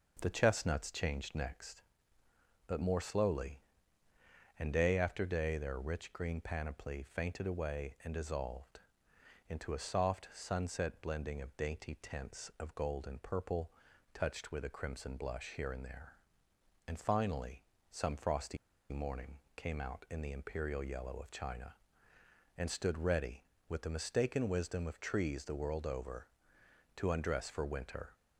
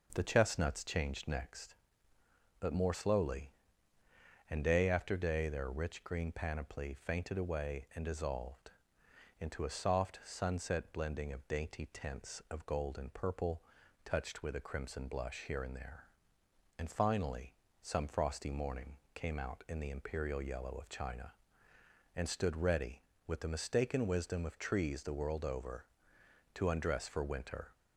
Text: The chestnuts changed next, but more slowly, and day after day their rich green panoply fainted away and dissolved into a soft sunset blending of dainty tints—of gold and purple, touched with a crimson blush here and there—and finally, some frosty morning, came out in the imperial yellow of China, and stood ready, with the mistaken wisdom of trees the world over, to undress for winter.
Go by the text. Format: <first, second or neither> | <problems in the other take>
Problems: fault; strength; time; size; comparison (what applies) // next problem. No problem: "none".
second | pauses between "dissolved" and "into"; noticeable; at 8.7 s; 0.68 s long; noticeable in the second // pauses between "frosty" and "morning"; slight; at 18.5 s; 0.35 s long